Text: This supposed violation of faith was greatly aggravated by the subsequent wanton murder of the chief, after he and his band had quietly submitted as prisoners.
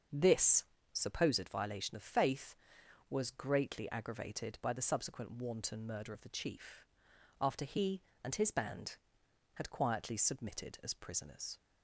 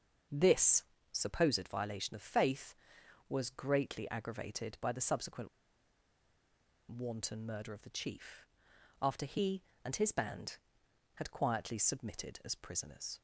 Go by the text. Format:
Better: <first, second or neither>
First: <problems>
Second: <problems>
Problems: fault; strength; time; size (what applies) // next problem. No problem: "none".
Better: first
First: starts louder than the rest; until 1.3 s; 6.5 dB // pauses between "This" and "supposed"; slight; at 0.6 s; 0.28 s long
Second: starts louder than the rest; until 1.5 s; 6.5 dB // pauses between "This" and "supposed"; slight; at 0.8 s; 0.28 s long // pauses between "subsequent" and "wanton"; strong; at 5.4 s; 1.4 s long